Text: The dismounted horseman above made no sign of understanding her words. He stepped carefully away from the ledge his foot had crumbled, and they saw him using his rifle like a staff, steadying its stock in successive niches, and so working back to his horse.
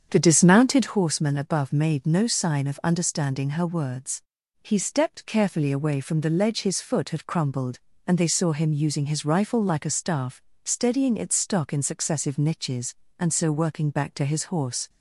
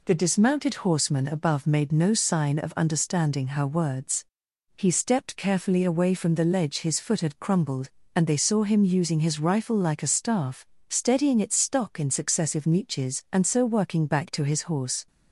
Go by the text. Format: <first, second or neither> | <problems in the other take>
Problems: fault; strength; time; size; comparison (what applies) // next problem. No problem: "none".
second | starts louder than the rest; strong; until 1.0 s; 7.5 dB